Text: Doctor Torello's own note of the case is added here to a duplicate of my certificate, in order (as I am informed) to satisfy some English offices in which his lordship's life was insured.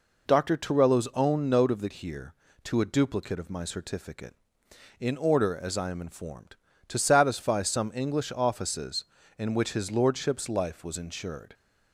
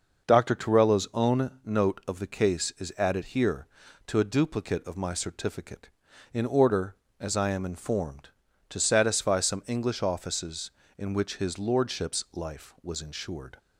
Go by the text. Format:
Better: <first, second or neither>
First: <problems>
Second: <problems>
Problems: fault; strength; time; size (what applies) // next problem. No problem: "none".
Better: second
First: skips "case is added"; at 1.8 s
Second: none